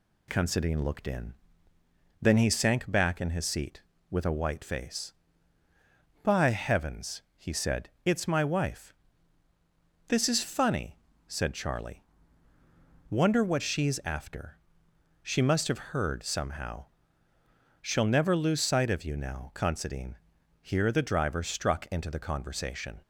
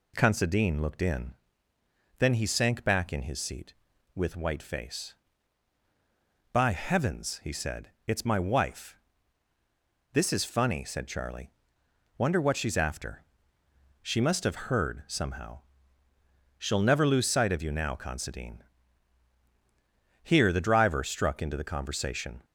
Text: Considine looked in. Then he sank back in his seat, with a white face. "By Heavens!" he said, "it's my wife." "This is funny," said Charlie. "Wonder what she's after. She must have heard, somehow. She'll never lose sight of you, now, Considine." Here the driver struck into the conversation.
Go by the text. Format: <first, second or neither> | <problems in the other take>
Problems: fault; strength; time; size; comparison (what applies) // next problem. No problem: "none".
first | skips "a"; at 4.3 s